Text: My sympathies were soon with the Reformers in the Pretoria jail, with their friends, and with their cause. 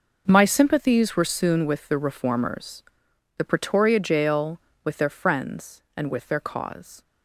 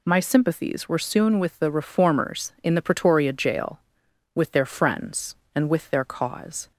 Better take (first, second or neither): second